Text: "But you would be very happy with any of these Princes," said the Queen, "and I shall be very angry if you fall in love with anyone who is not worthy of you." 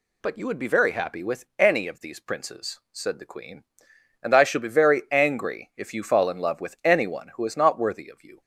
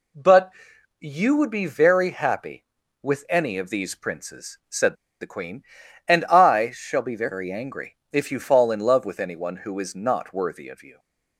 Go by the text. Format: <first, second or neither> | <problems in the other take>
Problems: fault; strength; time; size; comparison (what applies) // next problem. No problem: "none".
first | pauses between "But" and "you"; noticeable; at 0.5 s; 0.48 s long // pauses between "said" and "the"; slight; at 4.9 s; 0.25 s long // pauses between "angry" and "if"; slight; at 7.9 s; 0.16 s long